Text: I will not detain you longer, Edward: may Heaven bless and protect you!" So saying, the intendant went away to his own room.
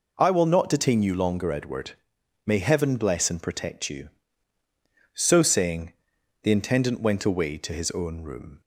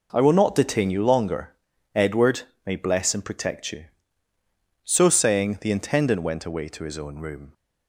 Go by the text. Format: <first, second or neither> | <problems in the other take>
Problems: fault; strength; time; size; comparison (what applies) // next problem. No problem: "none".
first | skips "Heaven"; at 2.7 s